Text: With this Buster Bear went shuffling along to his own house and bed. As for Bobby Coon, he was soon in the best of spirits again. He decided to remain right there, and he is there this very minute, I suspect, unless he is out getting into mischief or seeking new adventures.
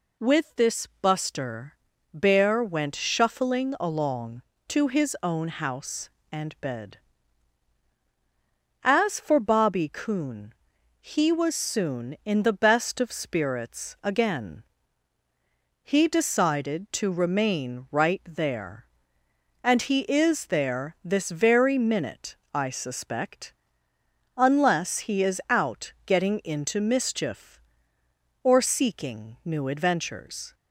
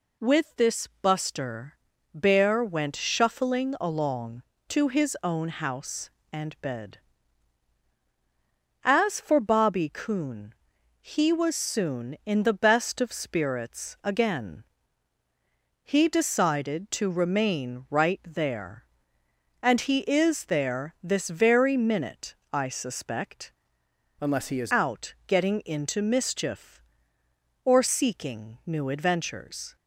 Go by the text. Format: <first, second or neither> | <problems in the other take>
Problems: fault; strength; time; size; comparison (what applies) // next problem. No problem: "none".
first | pauses between "this" and "Buster"; slight; at 0.8 s; 0.16 s long; slight in the first // pauses between "Buster" and "Bear"; at 1.7 s; 0.40 s long; also in the first // changes voice from "unless" to "is"; from 24.1 to 24.7 s; 0.6 s long